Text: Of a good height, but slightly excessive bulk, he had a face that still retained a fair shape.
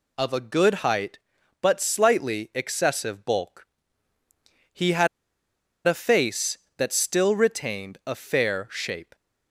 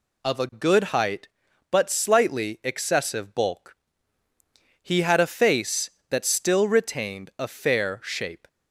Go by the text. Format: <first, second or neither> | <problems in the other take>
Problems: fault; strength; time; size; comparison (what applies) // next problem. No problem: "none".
second | pauses between "had" and "a"; noticeable; at 5.0 s; 0.79 s long